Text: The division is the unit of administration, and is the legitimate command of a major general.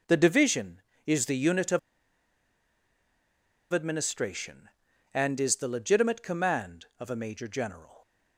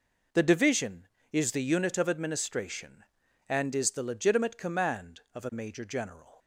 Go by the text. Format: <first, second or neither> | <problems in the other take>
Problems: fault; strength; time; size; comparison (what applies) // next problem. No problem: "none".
second | pauses between "of" and "administration"; strong; at 1.7 s; 1.9 s long